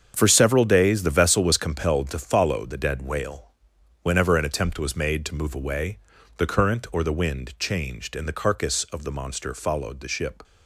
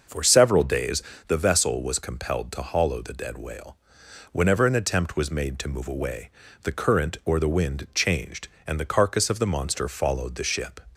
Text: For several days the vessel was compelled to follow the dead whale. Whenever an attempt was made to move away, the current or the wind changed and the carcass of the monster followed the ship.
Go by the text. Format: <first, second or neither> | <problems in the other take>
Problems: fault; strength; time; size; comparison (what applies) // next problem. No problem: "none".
first | starts louder than the rest; noticeable; until 1.3 s; 6 dB; strong in the first // pauses between "days" and "the"; slight; at 1.0 s; 0.24 s long // says "hollow" for "follow"; at 2.6 s